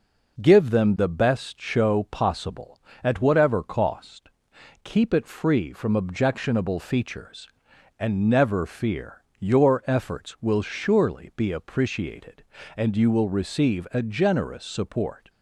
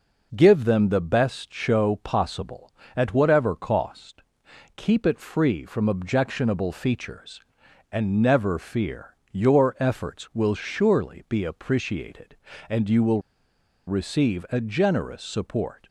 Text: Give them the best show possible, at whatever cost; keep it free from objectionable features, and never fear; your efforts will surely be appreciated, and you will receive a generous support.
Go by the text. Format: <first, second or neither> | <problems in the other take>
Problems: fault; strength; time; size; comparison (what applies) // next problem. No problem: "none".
first | pauses between "will" and "receive"; noticeable; at 13.2 s; 0.66 s long